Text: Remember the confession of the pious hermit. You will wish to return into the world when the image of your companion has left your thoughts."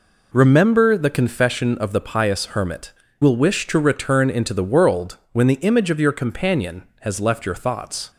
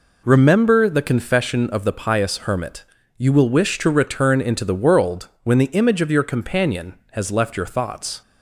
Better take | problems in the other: second | skips "You"; at 3.0 s

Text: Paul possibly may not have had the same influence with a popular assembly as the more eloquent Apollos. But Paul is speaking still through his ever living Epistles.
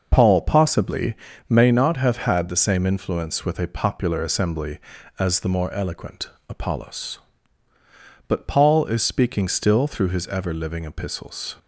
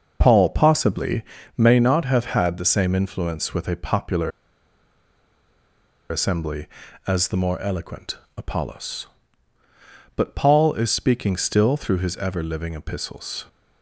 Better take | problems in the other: first | pauses between "possibly" and "may"; slight; at 1.2 s; 0.34 s long; slight in the first // pauses between "popular" and "assembly"; strong; at 4.3 s; 1.7 s long // pauses between "eloquent" and "Apollos"; slight; at 8.1 s; 0.22 s long; slight in the first

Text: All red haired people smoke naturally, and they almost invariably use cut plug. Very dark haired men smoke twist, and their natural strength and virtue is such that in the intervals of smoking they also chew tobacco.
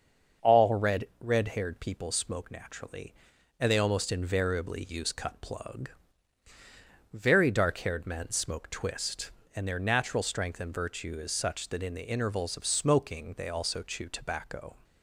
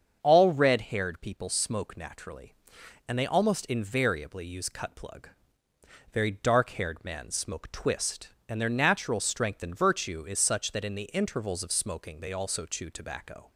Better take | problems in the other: second | starts louder than the rest; until 1.5 s; 6.5 dB; also in the second // says "red" twice; at 1.1 s

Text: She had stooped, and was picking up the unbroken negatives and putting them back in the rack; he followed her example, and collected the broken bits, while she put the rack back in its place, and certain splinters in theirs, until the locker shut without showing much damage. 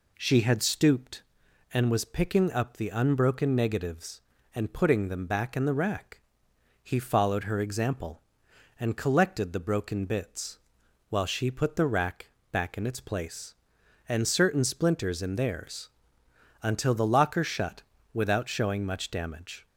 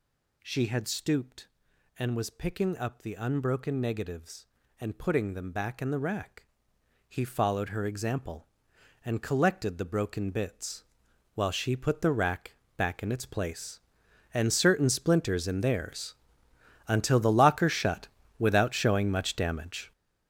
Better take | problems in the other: first | gets louder; strong; throughout; 10 dB // pauses between "rack" and "back"; slight; at 12.5 s; 0.22 s long; slight in the first // pauses between "shut" and "without"; slight; at 18.0 s; 0.30 s long; slight in the first

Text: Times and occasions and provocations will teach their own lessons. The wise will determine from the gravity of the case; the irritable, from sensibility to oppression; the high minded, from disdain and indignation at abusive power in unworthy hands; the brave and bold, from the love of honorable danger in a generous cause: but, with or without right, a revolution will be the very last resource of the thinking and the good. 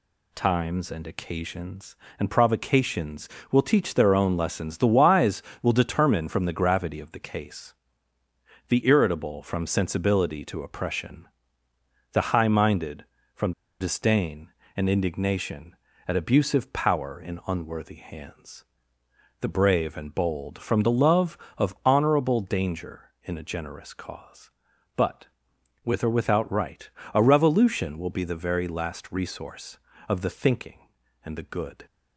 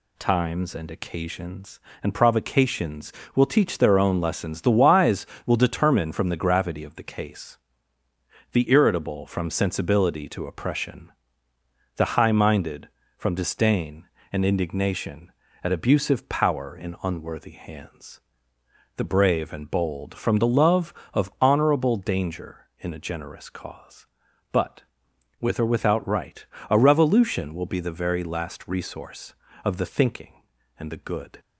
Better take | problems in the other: second | pauses between "from" and "disdain"; slight; at 13.5 s; 0.28 s long

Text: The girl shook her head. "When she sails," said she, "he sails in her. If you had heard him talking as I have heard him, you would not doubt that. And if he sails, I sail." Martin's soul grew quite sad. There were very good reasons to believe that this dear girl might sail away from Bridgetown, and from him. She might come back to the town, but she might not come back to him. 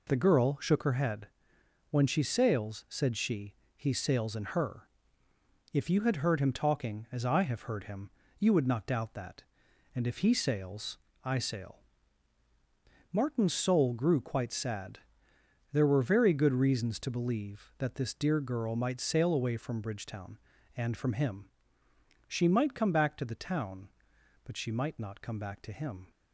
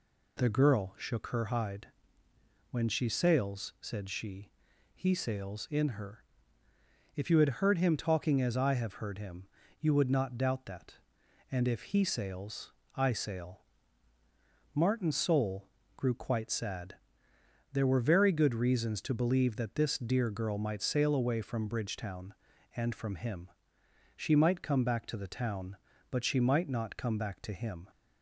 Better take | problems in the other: first | says "hide" for "head"; at 1.4 s // pauses between "soul" and "grew"; slight; at 15.6 s; 0.28 s long

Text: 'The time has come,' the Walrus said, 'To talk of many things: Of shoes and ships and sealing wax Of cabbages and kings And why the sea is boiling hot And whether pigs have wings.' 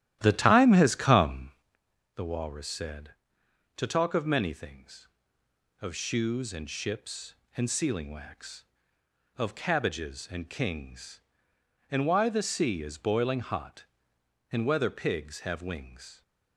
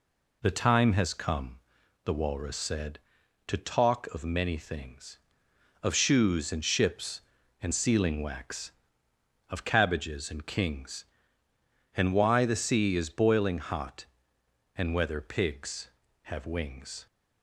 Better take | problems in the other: second | starts louder than the rest; strong; until 1.7 s; 13 dB

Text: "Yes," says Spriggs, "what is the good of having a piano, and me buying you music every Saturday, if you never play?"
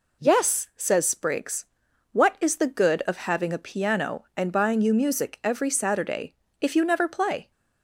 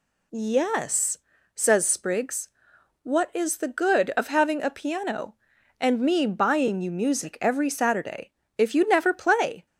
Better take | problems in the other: second | skips "me"; at 4.5 s

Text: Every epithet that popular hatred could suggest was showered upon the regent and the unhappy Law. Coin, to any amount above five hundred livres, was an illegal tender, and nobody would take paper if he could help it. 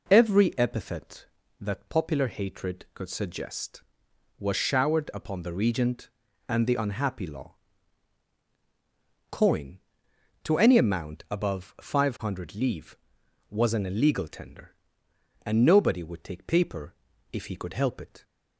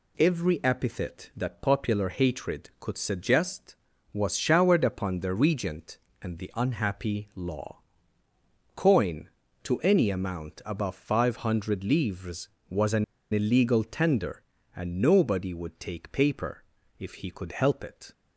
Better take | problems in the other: first | pauses between "an" and "illegal"; slight; at 13.0 s; 0.28 s long // pauses between "paper" and "if"; slight; at 16.6 s; 0.34 s long; slight in the first

